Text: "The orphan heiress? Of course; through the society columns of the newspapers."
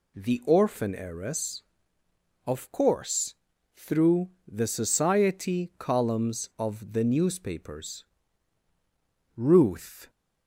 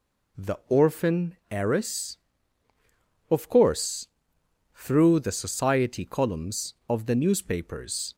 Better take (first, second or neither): second